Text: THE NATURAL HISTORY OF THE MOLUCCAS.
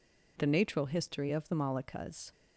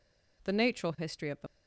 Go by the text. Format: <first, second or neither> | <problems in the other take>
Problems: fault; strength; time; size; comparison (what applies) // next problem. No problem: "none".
first | stops before "MOLUCCAS"; at 1.4 s